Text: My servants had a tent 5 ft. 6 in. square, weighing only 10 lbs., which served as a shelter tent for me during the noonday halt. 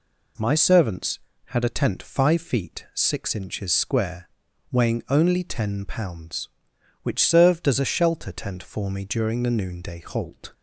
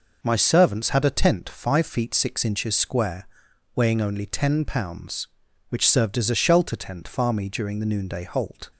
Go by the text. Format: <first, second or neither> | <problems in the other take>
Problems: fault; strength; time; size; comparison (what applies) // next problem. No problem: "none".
first | says "far" for "for"; at 7.0 s